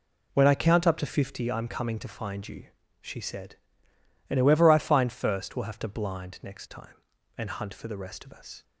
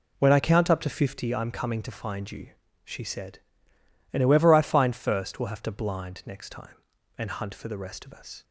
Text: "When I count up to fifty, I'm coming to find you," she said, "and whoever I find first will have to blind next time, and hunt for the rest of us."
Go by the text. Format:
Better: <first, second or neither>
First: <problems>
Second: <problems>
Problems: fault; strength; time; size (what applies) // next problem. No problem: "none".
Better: neither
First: none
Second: none